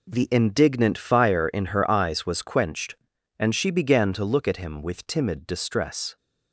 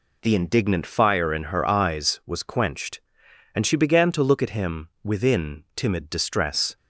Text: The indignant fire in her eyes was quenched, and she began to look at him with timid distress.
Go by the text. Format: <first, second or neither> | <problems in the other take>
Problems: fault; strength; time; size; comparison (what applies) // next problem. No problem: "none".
first | says "within" for "with"; at 5.0 s